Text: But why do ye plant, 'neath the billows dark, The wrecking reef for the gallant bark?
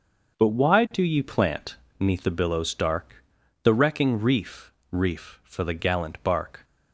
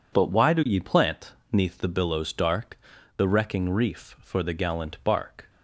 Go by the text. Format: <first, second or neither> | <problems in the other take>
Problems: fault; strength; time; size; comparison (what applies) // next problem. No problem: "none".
second | starts louder than the rest; until 1.4 s; 6.5 dB // says "reef" twice; at 4.9 s